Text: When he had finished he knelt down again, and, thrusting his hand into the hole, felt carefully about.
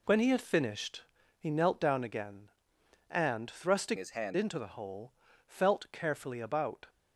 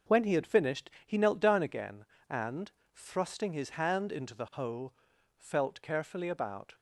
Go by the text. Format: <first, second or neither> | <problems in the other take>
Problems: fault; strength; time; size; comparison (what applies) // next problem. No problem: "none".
second | pauses between "finished" and "he"; slight; at 1.0 s; 0.34 s long; slight in the second // changes voice from "his" to "hand"; from 3.9 to 4.3 s; 0.4 s long